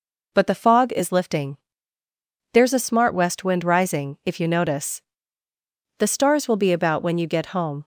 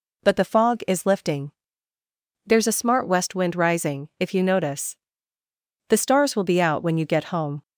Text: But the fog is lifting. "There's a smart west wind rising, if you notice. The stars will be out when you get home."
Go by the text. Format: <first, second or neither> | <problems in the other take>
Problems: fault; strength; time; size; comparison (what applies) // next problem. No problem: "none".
second | says "about" for "out"; at 6.7 s